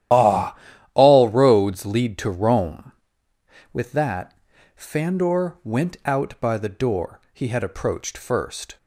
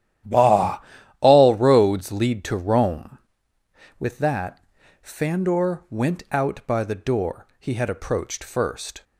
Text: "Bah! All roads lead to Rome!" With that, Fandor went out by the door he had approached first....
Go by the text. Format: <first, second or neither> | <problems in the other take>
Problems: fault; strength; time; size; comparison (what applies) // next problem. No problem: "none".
second | loses the start of "Bah"; at 0.1 s; 120 ms // starts louder than the rest; strong; until 1.5 s; 12 dB; strong in the second